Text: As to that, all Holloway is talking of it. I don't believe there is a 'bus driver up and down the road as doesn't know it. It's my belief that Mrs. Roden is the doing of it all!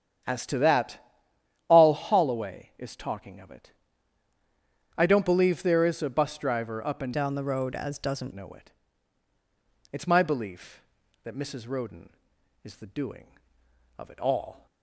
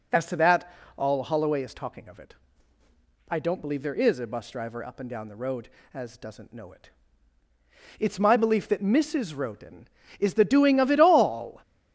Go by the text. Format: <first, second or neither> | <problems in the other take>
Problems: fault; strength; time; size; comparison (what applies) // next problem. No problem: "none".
second | starts louder than the rest; strong; until 1.9 s; 9 dB // changes voice from "down" to "doesn't"; from 7.1 to 8.3 s; 1.2 s long